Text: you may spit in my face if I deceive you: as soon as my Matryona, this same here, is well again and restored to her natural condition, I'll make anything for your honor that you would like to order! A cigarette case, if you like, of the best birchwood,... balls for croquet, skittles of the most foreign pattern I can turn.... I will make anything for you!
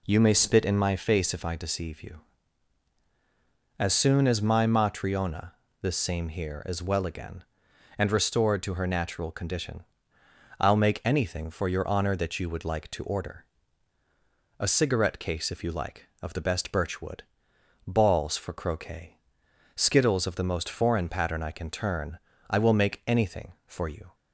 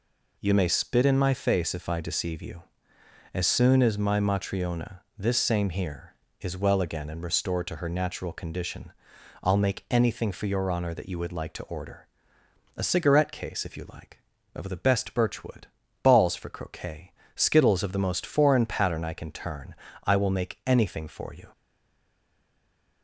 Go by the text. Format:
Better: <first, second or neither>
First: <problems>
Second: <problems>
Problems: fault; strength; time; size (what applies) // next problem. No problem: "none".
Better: first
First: none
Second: stays silent after the last word; noticeable; from 21.5 s on; 1.5 s long